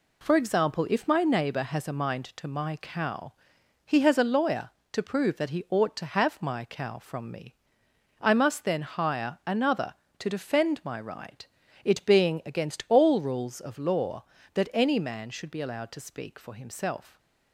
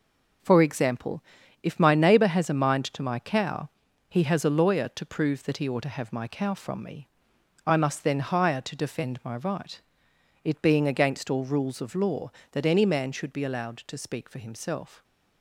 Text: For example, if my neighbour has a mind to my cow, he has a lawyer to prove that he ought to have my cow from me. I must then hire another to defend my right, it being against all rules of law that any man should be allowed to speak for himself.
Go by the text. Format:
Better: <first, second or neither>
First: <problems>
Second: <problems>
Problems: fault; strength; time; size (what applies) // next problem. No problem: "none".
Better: first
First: none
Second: skips "another"; at 8.6 s